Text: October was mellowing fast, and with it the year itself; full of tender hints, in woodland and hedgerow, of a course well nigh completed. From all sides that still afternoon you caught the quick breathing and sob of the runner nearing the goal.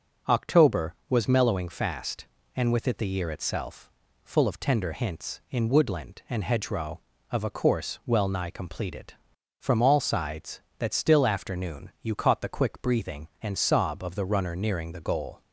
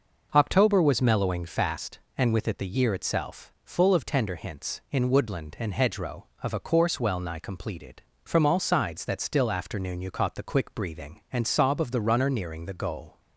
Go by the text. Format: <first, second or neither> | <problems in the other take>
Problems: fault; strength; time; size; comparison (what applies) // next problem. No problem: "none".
neither | none